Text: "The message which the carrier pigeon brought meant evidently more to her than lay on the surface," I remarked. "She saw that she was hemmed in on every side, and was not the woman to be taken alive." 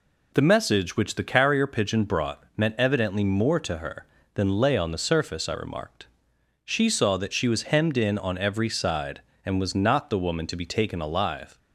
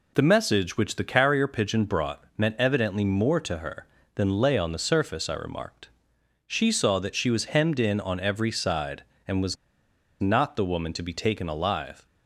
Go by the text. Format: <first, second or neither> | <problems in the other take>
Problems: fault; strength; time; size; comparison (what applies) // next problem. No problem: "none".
first | pauses between "was" and "not"; noticeable; at 9.5 s; 0.65 s long